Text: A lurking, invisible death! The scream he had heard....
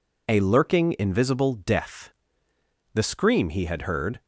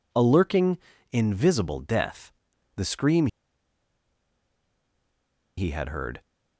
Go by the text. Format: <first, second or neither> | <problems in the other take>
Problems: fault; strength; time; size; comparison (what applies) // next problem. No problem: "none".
first | pauses between "scream" and "he"; strong; at 3.2 s; 2.3 s long